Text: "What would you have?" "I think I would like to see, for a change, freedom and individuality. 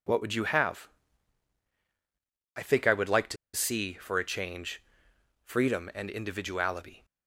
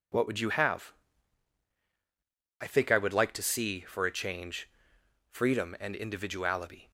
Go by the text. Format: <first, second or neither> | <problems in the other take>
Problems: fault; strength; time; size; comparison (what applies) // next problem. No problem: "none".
second | pauses between "to" and "see"; slight; at 3.3 s; 0.18 s long